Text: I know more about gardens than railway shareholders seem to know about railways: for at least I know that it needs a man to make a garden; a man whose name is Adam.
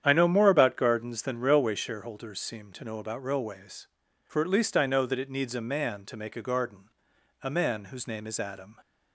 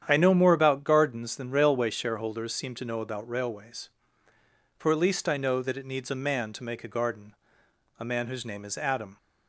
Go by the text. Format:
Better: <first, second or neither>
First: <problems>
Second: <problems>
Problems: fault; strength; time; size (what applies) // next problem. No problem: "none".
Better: neither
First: starts louder than the rest; strong; until 1.0 s; 9 dB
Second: starts louder than the rest; strong; until 1.0 s; 9 dB